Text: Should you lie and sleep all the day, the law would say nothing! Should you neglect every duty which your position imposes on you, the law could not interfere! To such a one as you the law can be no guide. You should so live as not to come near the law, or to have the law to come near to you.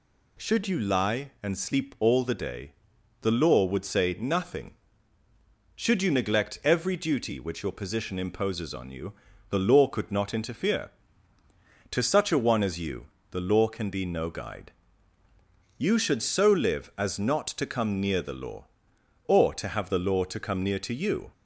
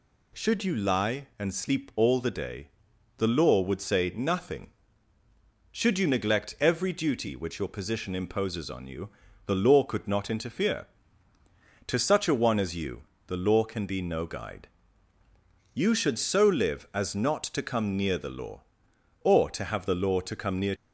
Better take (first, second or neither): first